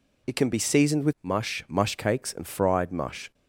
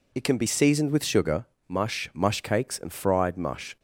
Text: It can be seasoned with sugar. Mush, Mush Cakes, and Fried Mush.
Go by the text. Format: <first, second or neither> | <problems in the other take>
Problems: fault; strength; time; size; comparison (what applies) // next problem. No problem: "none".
second | skips "sugar"; at 1.1 s